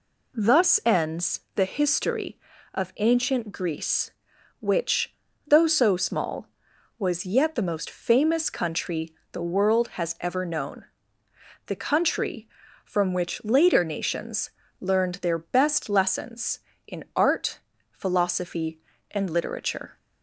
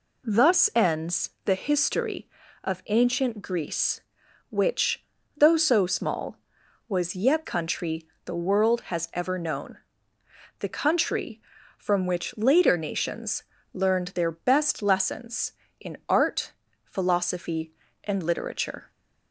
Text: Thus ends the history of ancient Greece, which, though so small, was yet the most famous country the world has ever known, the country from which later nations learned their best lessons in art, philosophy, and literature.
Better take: first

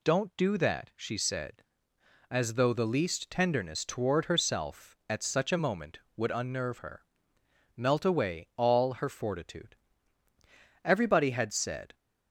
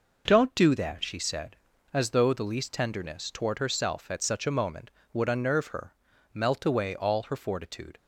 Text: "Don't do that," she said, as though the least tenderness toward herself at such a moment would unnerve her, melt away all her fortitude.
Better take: second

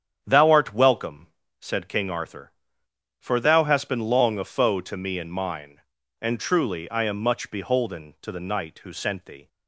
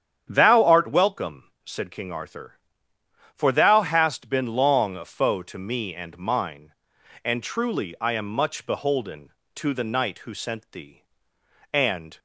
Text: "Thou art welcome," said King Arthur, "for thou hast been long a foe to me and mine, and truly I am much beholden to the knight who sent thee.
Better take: first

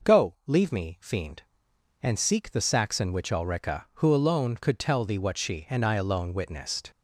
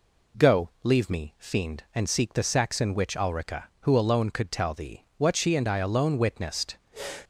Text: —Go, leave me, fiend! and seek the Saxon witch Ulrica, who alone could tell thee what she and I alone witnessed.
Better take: neither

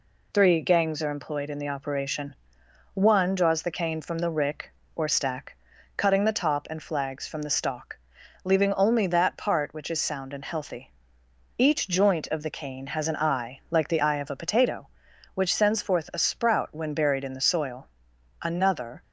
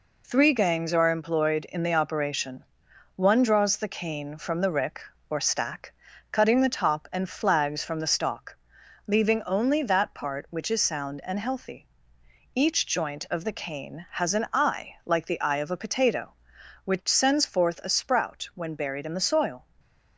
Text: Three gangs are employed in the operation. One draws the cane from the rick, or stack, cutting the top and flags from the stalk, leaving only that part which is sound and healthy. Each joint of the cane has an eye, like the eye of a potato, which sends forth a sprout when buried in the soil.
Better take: second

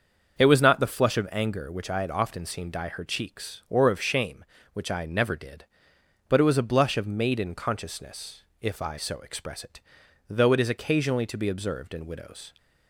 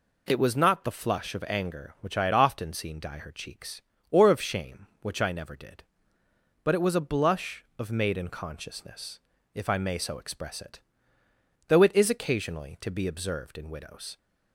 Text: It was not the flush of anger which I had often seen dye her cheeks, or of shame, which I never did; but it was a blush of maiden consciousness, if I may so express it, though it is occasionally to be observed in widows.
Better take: second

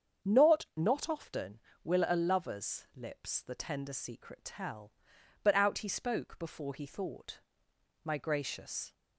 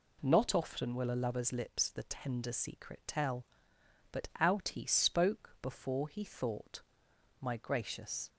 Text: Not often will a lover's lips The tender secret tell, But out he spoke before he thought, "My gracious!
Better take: second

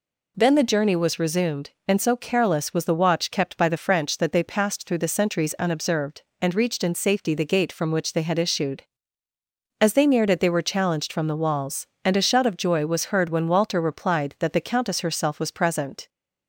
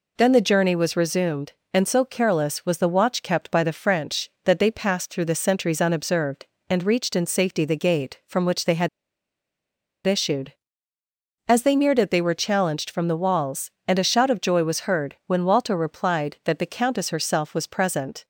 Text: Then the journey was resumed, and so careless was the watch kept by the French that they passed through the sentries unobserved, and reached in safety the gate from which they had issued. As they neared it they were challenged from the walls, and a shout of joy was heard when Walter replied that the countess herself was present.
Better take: first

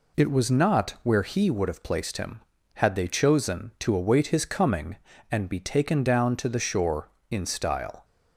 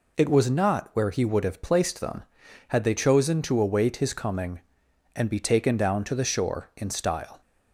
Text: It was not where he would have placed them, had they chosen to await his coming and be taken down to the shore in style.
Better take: second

